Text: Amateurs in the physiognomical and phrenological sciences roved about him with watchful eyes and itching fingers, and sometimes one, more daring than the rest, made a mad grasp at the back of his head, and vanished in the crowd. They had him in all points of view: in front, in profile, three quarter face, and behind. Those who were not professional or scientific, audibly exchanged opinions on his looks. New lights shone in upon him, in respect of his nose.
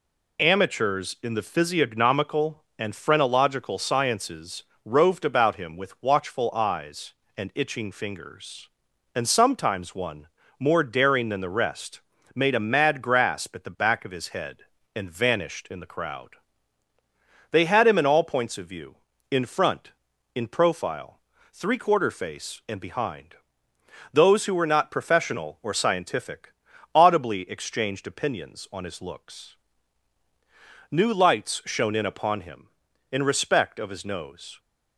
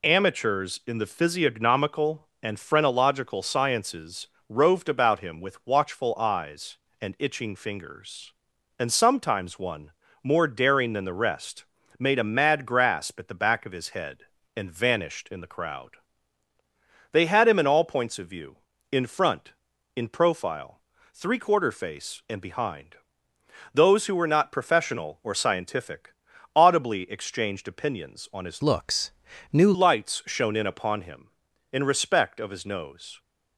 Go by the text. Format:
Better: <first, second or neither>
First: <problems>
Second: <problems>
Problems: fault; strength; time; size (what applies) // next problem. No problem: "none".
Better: first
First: pauses between "sciences" and "roved"; slight; at 4.6 s; 0.24 s long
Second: pauses between "sciences" and "roved"; slight; at 4.2 s; 0.24 s long // changes voice from "looks" to "New"; from 28.6 to 29.7 s; 1.1 s long